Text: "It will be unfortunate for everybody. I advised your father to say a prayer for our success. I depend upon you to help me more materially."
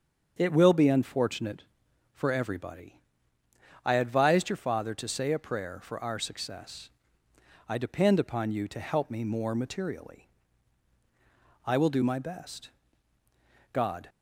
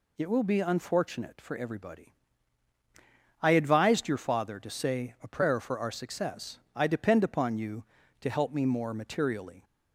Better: second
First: starts louder than the rest; until 1.3 s; 7 dB // goes on to say "I will do my best God"; strong; from 11.6 s on; 2.4 s long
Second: none

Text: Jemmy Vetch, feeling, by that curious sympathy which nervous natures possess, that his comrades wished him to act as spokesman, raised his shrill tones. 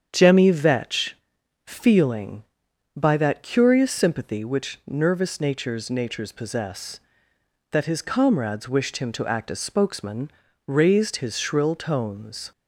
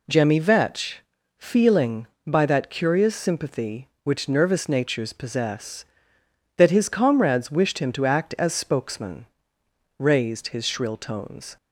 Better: second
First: starts louder than the rest; strong; until 1.1 s; 8 dB // says "natures" twice; at 5.9 s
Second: none

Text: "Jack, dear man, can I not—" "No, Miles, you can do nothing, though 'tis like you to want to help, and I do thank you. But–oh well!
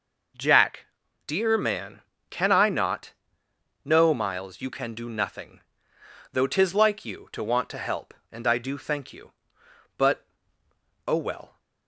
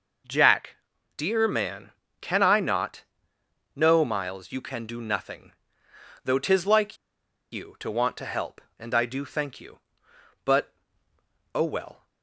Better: first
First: none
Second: pauses between "like" and "you"; noticeable; at 6.9 s; 0.56 s long

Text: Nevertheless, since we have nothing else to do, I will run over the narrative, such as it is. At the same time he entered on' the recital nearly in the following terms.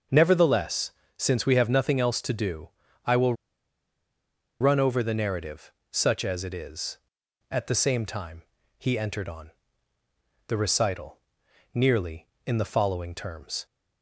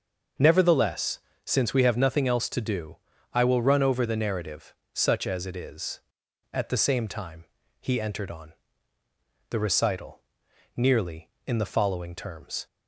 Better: second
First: starts louder than the rest; until 1.3 s; 6.5 dB // pauses between "will" and "run"; strong; at 3.3 s; 1.2 s long // pauses between "time" and "he"; slight; at 8.4 s; 0.36 s long // pauses between "on" and "the"; noticeable; at 9.5 s; 0.96 s long // pauses between "recital" and "nearly"; noticeable; at 11.1 s; 0.54 s long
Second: starts louder than the rest; until 1.6 s; 6.5 dB // pauses between "time" and "he"; slight; at 7.4 s; 0.36 s long // pauses between "on" and "the"; noticeable; at 8.5 s; 0.96 s long // pauses between "recital" and "nearly"; noticeable; at 10.2 s; 0.54 s long

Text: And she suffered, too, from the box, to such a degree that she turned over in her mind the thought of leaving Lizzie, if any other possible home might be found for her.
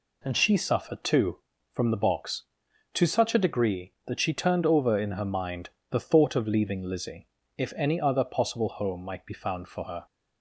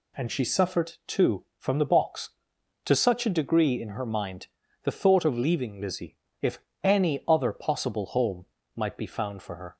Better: first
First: pauses between "mind" and "the"; slight; at 5.6 s; 0.20 s long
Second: skips "that she turned over"; at 3.8 s // pauses between "mind" and "the"; slight; at 4.4 s; 0.36 s long // pauses between "if" and "any"; slight; at 6.5 s; 0.24 s long // pauses between "home" and "might"; slight; at 8.4 s; 0.32 s long

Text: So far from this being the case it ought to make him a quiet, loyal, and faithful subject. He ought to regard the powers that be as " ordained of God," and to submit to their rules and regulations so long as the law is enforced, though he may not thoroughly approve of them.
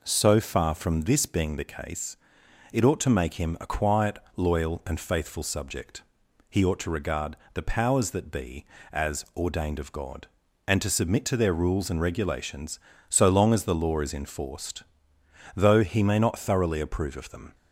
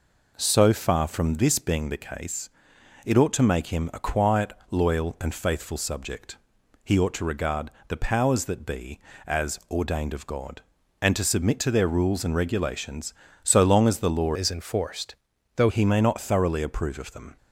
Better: first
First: pauses between "case" and "it"; noticeable; at 2.1 s; 0.54 s long // pauses between "regard" and "the"; slight; at 7.3 s; 0.16 s long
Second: pauses between "case" and "it"; noticeable; at 2.4 s; 0.54 s long // pauses between "regard" and "the"; slight; at 7.7 s; 0.16 s long // changes voice from "is" to "though"; from 14.3 to 15.6 s; 1.3 s long

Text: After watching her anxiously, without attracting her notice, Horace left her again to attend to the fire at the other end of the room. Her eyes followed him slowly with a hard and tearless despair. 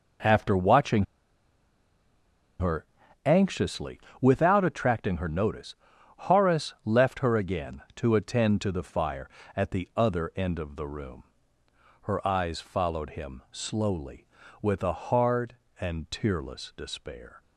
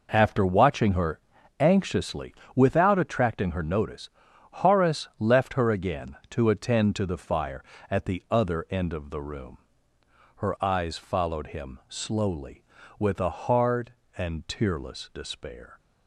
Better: second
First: pauses between "watching" and "her"; strong; at 1.0 s; 1.5 s long // pauses between "her" and "anxiously"; at 2.8 s; 0.40 s long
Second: pauses between "her" and "anxiously"; at 1.1 s; 0.40 s long

